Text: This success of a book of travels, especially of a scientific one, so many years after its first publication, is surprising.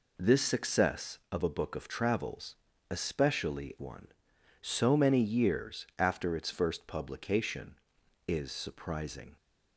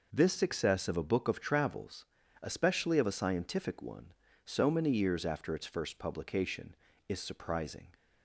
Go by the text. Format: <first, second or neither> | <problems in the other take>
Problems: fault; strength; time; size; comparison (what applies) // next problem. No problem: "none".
second | skips "of a scientific"; at 3.7 s